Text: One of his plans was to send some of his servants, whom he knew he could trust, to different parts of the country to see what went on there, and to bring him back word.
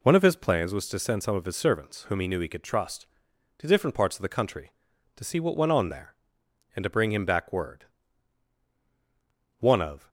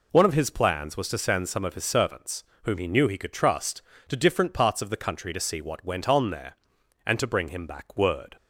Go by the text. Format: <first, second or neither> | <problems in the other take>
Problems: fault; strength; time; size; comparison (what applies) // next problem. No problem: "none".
second | goes on to say "One of"; from 9.5 s on; 0.50 s long